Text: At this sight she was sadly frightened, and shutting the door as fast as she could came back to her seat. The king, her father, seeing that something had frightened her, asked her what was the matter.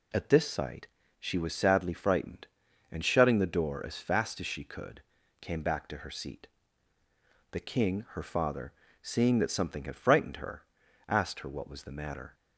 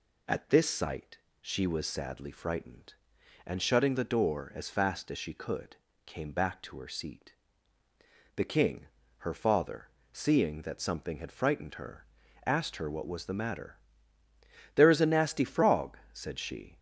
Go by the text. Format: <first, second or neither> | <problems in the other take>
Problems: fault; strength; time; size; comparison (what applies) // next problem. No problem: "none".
first | pauses between "sight" and "she"; slight; at 1.1 s; 0.22 s long; slight in the first // pauses between "could" and "came"; slight; at 5.7 s; 0.30 s long; also in the first // goes on to say "There is a nasty frog said she"; strong; from 14.7 s on; 2.0 s long